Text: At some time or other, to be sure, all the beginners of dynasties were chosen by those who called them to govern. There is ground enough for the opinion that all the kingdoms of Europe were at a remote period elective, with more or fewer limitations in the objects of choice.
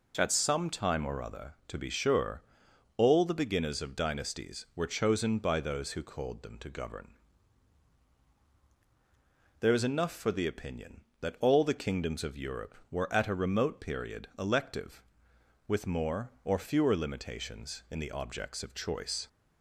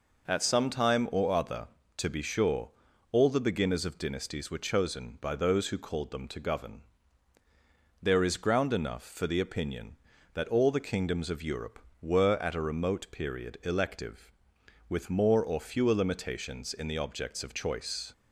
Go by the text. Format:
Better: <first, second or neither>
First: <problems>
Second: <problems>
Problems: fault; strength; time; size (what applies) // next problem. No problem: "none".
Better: second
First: skips "ground"; at 9.8 s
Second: none